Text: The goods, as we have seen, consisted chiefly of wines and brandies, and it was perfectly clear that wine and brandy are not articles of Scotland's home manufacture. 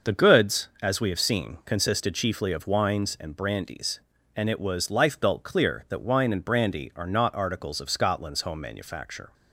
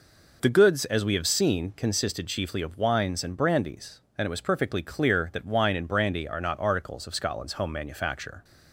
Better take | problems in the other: second | says "lifebelt" for "perfectly"; at 4.9 s

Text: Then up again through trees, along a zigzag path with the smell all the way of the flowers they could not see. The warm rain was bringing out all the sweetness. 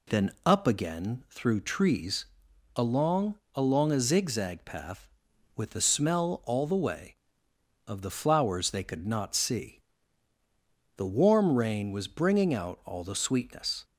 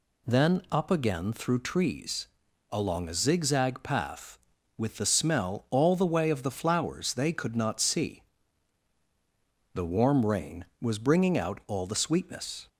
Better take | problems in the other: second | says "along" twice; at 3.5 s

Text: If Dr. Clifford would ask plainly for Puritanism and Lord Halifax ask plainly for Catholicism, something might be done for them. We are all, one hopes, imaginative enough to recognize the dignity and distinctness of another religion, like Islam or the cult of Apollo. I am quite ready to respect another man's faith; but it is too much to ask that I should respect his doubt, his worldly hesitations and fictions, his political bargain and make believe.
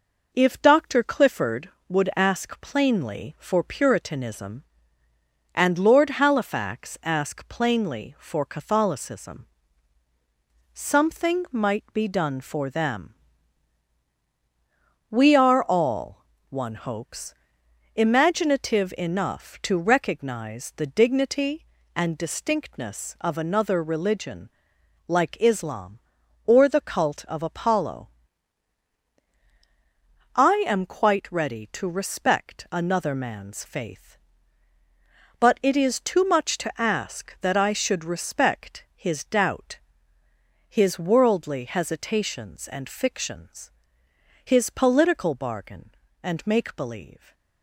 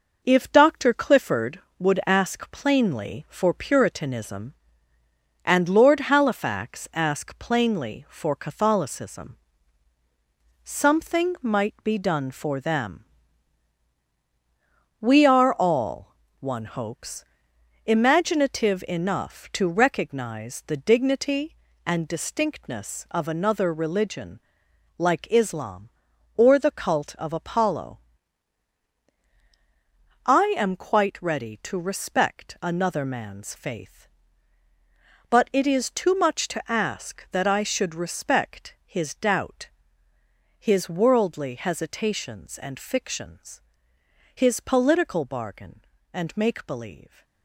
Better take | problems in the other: first | gets quieter; noticeable; throughout; 6 dB

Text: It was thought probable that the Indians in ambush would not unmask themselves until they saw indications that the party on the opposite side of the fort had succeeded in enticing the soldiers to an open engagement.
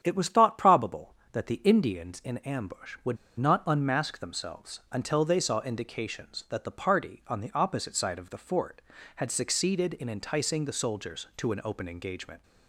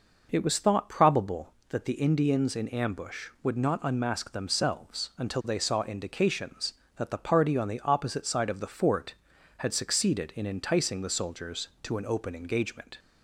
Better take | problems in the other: second | starts louder than the rest; strong; until 1.0 s; 9 dB // pauses between "would" and "not"; slight; at 3.1 s; 0.23 s long

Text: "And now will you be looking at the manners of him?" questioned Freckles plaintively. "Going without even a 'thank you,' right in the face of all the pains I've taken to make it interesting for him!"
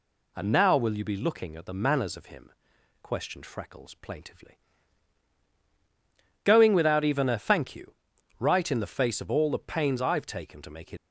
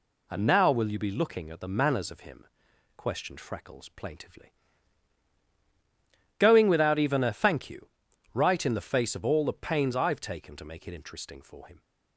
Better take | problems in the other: second | stops before "interesting for him"; at 10.9 s

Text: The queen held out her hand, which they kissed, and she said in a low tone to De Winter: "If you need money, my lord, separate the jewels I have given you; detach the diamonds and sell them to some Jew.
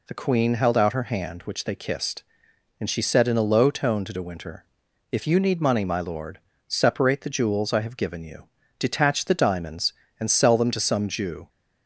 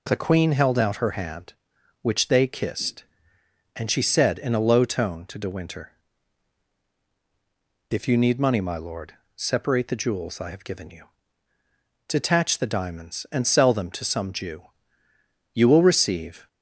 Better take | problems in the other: first | goes on to say "You will receive"; noticeable; from 15.5 s on; 0.94 s long

